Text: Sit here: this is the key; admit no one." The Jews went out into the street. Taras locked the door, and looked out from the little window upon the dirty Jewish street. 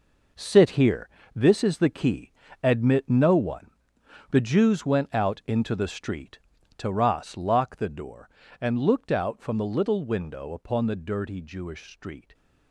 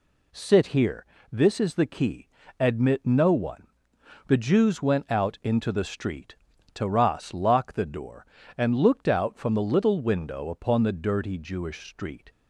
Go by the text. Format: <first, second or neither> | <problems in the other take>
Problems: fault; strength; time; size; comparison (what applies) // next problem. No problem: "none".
second | gets quieter; strong; throughout; 10.5 dB